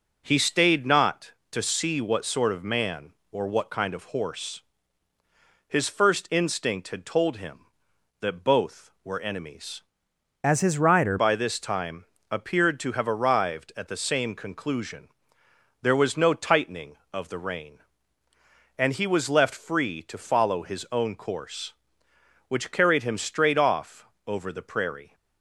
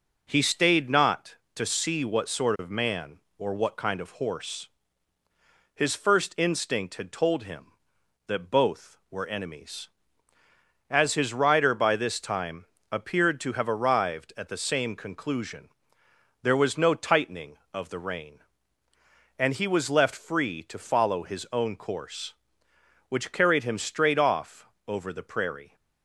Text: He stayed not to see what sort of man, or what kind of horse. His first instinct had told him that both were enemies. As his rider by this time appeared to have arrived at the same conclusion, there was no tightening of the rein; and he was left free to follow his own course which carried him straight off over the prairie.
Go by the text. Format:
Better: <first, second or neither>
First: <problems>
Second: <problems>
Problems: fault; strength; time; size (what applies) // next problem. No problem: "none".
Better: second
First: changes voice from "As" to "rider"; from 10.4 to 11.1 s; 0.7 s long // pauses between "time" and "appeared"; slight; at 12.0 s; 0.30 s long // pauses between "off" and "over"; slight; at 24.0 s; 0.22 s long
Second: pauses between "time" and "appeared"; slight; at 12.6 s; 0.30 s long // pauses between "off" and "over"; slight; at 24.6 s; 0.22 s long